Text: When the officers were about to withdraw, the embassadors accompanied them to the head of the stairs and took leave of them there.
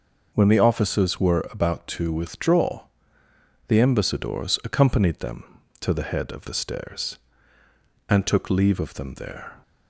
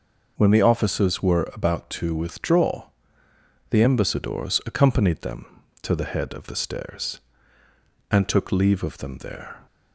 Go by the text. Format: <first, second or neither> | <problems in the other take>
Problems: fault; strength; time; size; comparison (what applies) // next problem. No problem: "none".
neither | none